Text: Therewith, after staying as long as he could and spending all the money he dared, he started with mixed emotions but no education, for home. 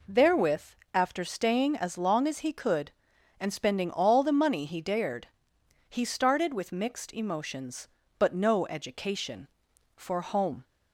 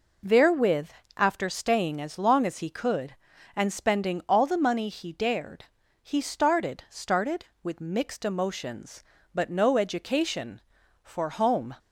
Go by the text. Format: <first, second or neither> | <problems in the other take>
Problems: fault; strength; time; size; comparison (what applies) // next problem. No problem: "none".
first | says "started" twice; at 6.8 s